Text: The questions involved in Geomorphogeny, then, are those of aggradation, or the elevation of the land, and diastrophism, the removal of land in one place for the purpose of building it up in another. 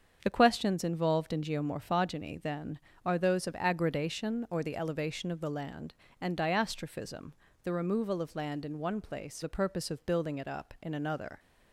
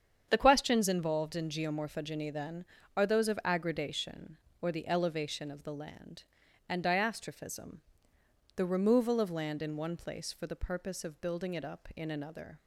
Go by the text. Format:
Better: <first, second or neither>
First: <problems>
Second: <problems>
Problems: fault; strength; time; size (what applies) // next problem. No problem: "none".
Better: second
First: starts louder than the rest; strong; until 1.2 s; 7 dB // skips "for"; at 9.4 s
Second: starts louder than the rest; strong; until 1.3 s; 8 dB